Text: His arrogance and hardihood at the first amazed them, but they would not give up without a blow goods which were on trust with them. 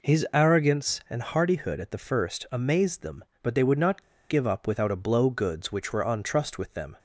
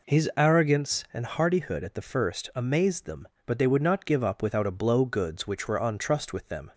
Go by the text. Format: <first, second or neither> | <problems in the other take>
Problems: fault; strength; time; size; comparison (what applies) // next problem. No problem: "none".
second | pauses between "not" and "give"; slight; at 4.0 s; 0.27 s long